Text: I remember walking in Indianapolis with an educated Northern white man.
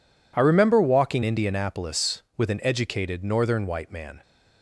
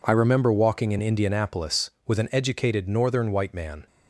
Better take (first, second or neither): second